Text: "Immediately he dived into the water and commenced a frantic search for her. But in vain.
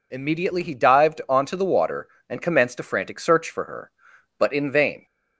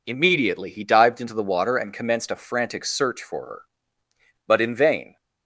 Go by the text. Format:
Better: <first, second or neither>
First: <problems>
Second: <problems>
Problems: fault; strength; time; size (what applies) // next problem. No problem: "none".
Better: second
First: says "onto" for "into"; at 1.2 s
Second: none